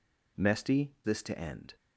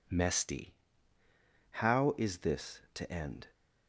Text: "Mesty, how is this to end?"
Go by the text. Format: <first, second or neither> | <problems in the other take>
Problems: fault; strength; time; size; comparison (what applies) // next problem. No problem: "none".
second | skips "how is"; at 0.9 s